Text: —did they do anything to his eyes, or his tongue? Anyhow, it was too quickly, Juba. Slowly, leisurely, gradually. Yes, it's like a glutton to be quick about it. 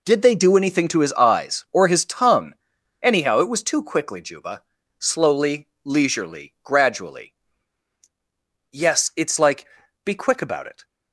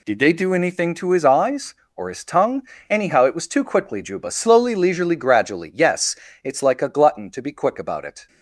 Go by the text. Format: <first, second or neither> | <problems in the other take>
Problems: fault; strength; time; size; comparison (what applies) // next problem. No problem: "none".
second | skips "a glutton to"; at 9.8 s